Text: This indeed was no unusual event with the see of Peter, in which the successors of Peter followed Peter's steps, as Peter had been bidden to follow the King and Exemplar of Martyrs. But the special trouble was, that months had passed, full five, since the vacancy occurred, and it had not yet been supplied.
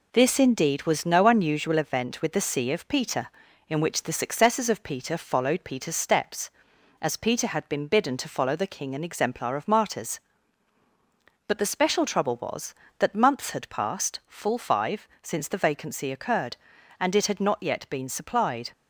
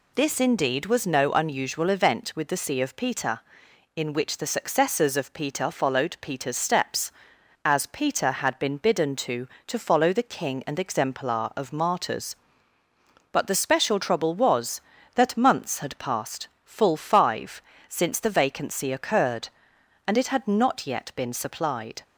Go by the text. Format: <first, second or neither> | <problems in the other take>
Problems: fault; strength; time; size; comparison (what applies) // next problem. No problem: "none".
first | says "to" twice; at 9.6 s